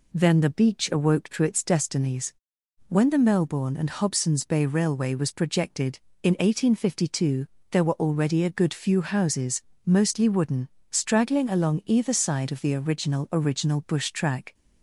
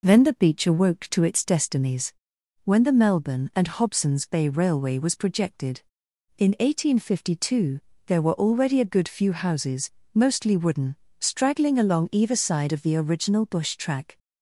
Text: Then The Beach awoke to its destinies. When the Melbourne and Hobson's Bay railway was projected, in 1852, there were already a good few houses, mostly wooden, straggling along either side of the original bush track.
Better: second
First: says "original" twice; at 13.3 s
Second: none

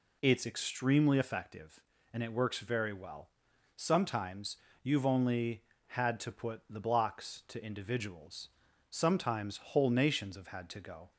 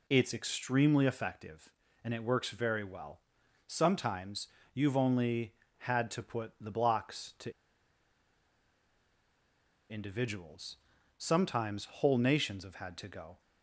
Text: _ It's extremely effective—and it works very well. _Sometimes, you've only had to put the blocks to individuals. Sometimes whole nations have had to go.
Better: first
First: none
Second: pauses between "to" and "individuals"; strong; at 7.5 s; 2.3 s long

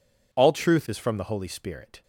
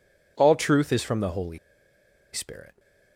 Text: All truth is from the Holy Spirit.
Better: first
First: none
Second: pauses between "Holy" and "Spirit"; noticeable; at 1.5 s; 0.74 s long

